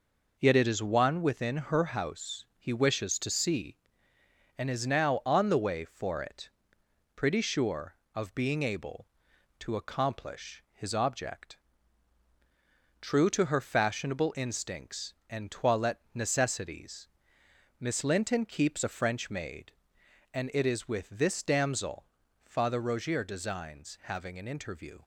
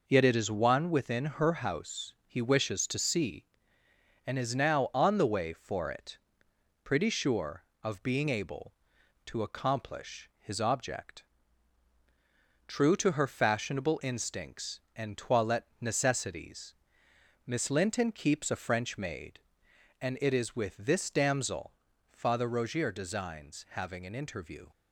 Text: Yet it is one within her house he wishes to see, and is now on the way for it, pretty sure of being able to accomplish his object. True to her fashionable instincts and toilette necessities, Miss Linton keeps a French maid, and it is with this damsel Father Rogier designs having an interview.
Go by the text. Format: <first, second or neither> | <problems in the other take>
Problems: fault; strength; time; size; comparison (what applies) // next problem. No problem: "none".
neither | pauses between "damsel" and "Father"; the same in both